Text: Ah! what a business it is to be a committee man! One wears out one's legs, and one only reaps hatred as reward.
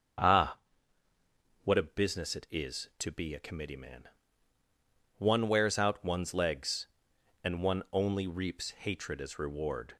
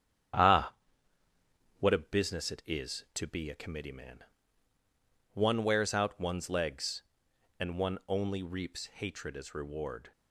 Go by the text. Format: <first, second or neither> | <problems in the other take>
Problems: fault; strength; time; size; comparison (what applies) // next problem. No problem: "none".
first | gets quieter; noticeable; throughout; 6 dB // starts louder than the rest; strong; until 2.4 s; 9.5 dB; also in the first